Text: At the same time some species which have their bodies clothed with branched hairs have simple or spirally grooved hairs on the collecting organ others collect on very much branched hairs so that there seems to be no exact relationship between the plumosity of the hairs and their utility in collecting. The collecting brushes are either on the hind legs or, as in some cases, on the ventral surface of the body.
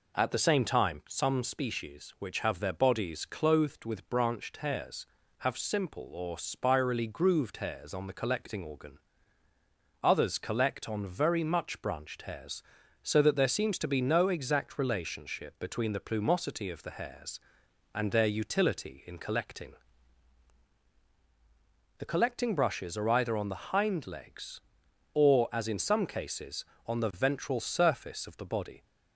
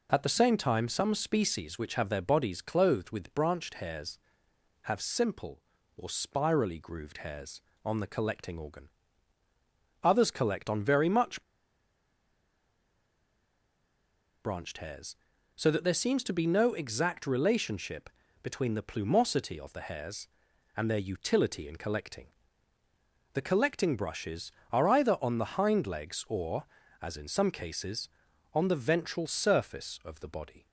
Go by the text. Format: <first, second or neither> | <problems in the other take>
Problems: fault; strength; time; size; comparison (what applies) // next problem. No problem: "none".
first | pauses between "organ" and "others"; at 8.8 s; 1.1 s long; also in the first // pauses between "much" and "branched"; strong; at 11.4 s; 3.0 s long // pauses between "relationship" and "between"; slight; at 18.0 s; 0.34 s long